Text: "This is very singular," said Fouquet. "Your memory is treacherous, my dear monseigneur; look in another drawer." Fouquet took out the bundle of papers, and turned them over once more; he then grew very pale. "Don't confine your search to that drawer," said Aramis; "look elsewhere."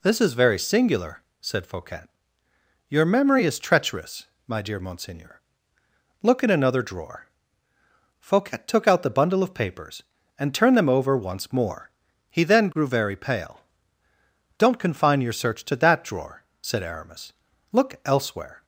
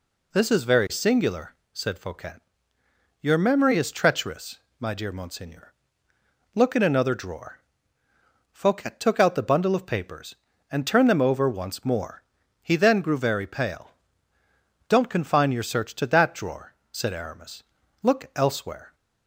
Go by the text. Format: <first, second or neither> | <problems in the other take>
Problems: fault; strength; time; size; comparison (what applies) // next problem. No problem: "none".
neither | none